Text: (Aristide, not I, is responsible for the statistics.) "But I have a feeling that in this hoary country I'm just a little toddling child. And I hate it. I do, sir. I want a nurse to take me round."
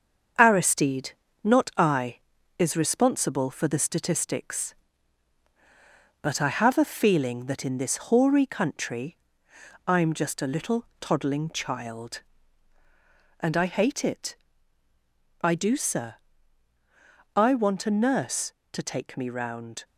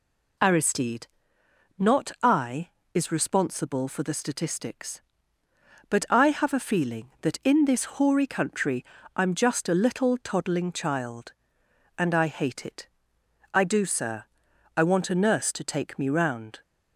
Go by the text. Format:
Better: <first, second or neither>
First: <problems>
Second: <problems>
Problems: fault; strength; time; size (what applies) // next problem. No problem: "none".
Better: second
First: gets quieter; noticeable; throughout; 5 dB // pauses between "country" and "I'm"; noticeable; at 9.1 s; 0.70 s long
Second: pauses between "country" and "I'm"; slight; at 8.8 s; 0.32 s long